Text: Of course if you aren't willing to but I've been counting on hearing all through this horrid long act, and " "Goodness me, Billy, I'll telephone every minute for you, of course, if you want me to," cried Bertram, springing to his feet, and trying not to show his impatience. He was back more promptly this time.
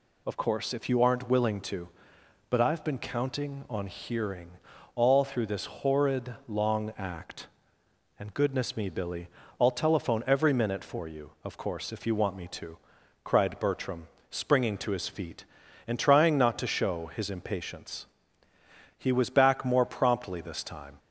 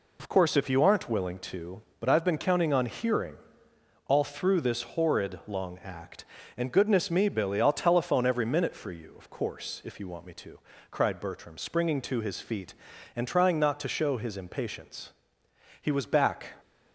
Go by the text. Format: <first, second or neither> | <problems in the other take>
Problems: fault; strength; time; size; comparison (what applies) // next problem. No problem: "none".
first | pauses between "hearing" and "all"; noticeable; at 3.3 s; 0.70 s long; noticeable in the first // stops before "more promptly this time"; at 16.5 s